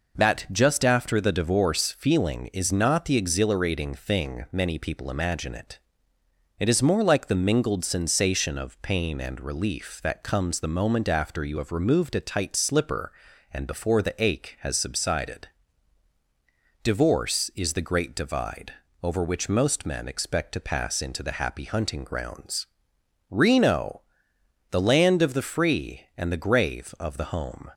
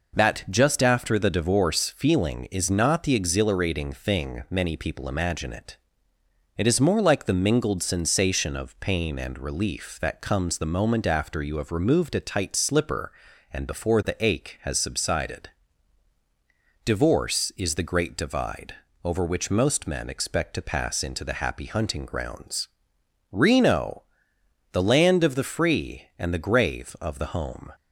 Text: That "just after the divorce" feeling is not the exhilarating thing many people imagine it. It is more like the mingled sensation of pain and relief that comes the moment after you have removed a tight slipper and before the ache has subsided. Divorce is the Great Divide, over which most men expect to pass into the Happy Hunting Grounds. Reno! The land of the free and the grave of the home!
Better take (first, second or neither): neither